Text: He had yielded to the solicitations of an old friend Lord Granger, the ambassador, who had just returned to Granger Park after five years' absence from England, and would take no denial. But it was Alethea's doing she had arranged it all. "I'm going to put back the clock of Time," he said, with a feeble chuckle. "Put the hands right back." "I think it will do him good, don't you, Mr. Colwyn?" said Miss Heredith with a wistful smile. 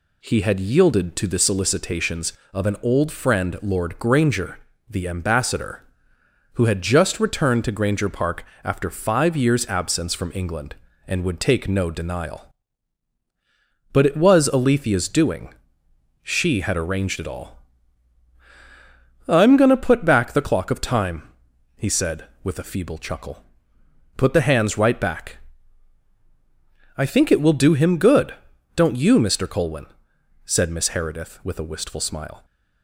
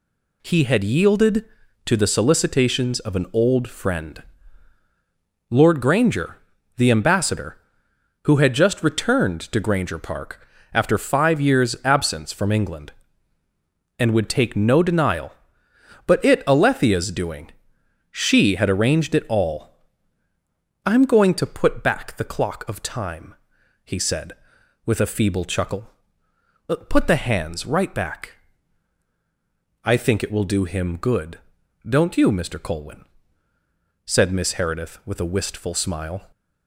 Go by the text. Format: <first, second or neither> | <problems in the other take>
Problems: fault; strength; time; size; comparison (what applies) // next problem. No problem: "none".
first | pauses between "friend" and "Lord"; strong; at 4.2 s; 1.2 s long // pauses between "Park" and "after"; slight; at 10.4 s; 0.26 s long; slight in the first // skips "was"; at 16.4 s // pauses between "doing" and "she"; noticeable; at 17.4 s; 0.62 s long; noticeable in the first